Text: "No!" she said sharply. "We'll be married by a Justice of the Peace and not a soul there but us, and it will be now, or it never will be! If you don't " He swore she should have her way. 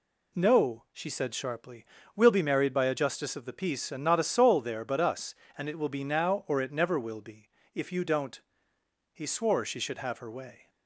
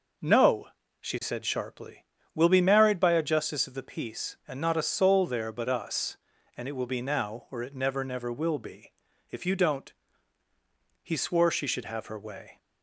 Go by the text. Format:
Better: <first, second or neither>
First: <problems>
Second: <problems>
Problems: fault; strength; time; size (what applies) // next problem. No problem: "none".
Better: first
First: none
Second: says "never" twice; at 8.0 s